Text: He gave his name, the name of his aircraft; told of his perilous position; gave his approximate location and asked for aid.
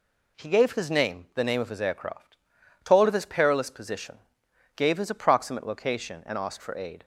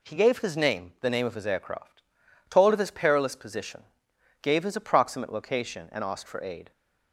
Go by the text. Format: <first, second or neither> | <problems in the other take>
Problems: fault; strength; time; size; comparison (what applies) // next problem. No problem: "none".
neither | none